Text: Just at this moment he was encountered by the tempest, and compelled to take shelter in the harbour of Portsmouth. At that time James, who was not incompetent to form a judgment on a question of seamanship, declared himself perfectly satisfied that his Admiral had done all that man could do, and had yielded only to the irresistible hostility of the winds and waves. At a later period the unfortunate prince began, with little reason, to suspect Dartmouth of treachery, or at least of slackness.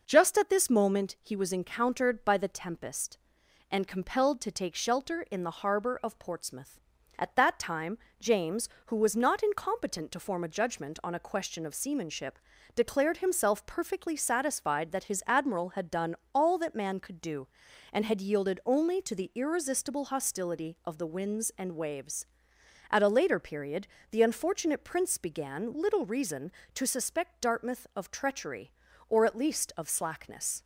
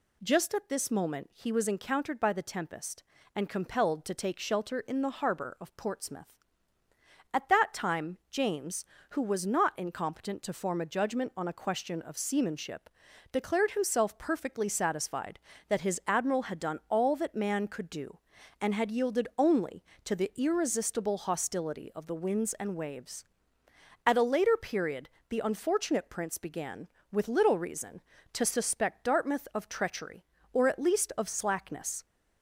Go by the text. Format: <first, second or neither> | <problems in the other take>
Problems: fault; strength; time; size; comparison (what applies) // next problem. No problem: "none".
second | pauses between "time" and "James"; slight; at 7.9 s; 0.22 s long // pauses between "done" and "all"; slight; at 16.1 s; 0.20 s long // pauses between "period" and "the"; slight; at 23.8 s; 0.24 s long; slight in the second // skips "with"; at 25.7 s